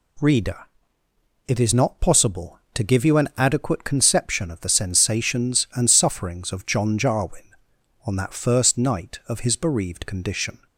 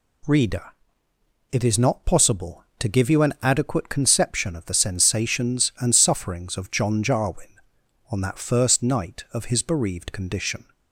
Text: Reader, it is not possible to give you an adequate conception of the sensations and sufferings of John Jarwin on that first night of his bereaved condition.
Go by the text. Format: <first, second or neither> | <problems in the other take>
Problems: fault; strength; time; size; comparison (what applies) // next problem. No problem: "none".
neither | none